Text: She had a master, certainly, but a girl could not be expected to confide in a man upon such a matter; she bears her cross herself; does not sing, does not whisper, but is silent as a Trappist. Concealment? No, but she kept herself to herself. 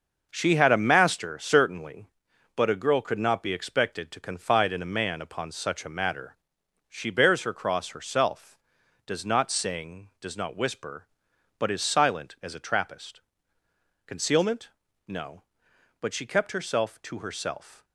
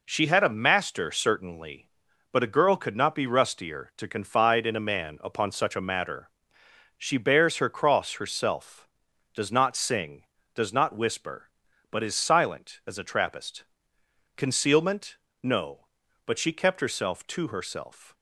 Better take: first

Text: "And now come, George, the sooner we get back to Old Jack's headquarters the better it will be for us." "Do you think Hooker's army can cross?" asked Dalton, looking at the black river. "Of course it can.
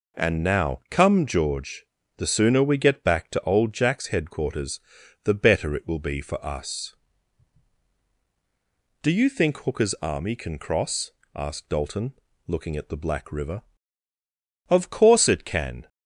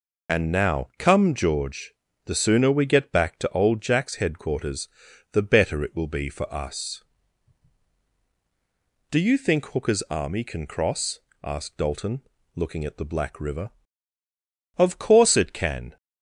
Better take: first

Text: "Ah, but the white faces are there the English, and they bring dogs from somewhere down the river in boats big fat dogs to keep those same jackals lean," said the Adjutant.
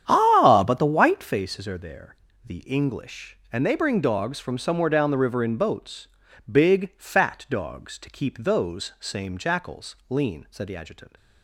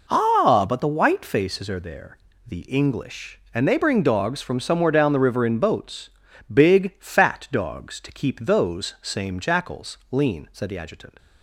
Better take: second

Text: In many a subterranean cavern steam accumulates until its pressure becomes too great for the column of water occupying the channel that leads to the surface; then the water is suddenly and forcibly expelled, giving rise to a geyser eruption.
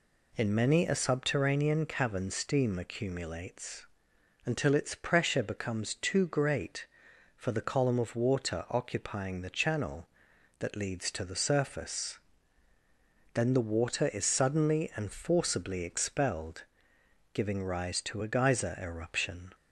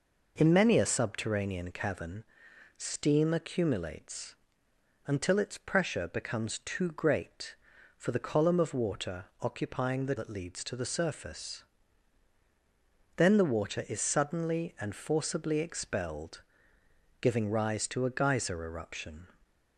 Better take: first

